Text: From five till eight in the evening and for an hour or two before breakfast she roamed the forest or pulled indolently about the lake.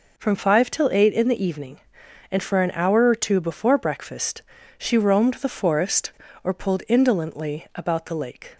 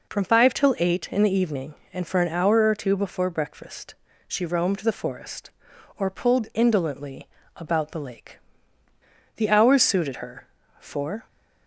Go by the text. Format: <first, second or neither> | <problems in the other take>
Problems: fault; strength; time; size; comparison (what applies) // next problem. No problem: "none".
first | pauses between "breakfast" and "she"; slight; at 3.9 s; 0.32 s long; slight in the first // pauses between "indolently" and "about"; slight; at 7.2 s; 0.30 s long // goes on to say "The hours suited her for"; strong; from 9.3 s on; 1.9 s long